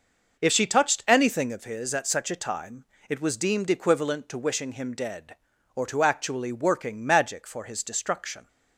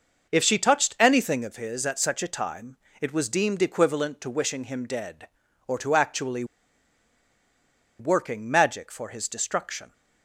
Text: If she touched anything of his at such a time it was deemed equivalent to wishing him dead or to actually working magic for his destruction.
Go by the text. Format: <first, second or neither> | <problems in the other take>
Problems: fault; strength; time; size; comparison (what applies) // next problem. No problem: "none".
first | pauses between "time" and "it"; slight; at 2.7 s; 0.24 s long; slight in the first // pauses between "actually" and "working"; strong; at 6.4 s; 1.5 s long